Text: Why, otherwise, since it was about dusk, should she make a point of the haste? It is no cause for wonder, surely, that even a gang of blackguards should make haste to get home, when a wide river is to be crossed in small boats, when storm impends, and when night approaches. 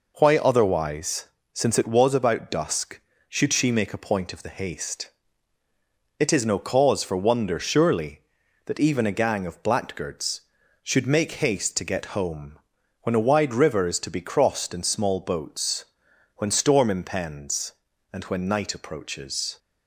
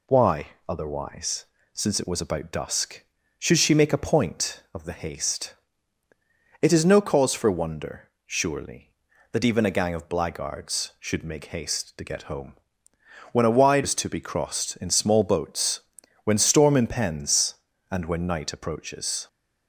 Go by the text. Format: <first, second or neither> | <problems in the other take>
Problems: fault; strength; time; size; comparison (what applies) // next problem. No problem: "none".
first | skips "river"; at 13.8 s